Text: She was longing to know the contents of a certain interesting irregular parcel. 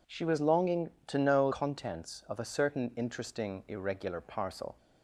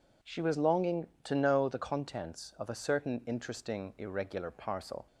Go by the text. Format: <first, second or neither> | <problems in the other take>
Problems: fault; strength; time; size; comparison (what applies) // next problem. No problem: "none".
second | skips "the"; at 1.5 s